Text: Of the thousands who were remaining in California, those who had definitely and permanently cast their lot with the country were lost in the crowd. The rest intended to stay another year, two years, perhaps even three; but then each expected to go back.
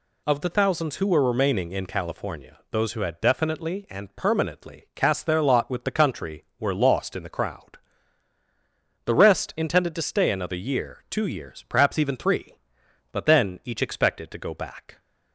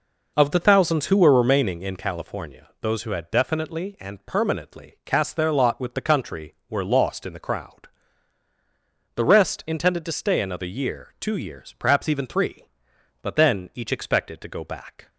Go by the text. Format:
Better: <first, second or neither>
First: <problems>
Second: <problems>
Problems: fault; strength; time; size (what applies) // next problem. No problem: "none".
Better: first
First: none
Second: starts louder than the rest; noticeable; until 1.7 s; 5 dB